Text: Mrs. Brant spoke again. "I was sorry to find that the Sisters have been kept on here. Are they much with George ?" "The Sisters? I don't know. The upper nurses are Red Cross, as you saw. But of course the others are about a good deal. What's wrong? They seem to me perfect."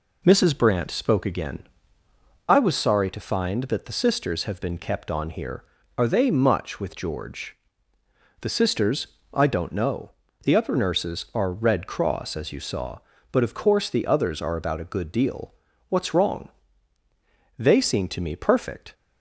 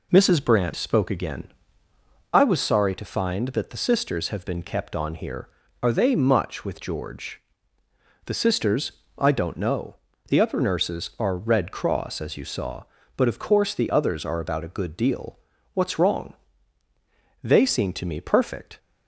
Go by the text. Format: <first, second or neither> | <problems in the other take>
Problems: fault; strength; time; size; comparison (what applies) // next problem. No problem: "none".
neither | none